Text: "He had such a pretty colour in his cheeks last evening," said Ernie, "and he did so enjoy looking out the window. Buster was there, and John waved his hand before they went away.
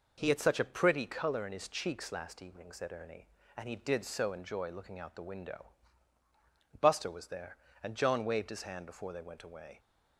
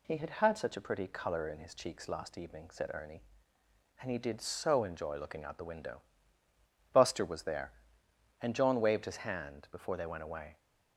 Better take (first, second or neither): first